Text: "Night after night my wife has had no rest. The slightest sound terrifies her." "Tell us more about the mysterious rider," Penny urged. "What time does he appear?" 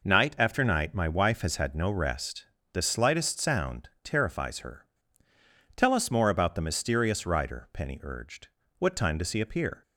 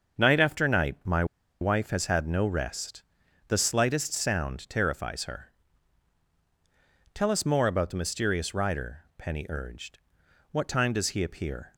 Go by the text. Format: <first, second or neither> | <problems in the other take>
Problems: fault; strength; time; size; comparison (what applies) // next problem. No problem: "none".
first | starts louder than the rest; until 1.6 s; 6.5 dB // pauses between "my" and "wife"; at 1.2 s; 0.36 s long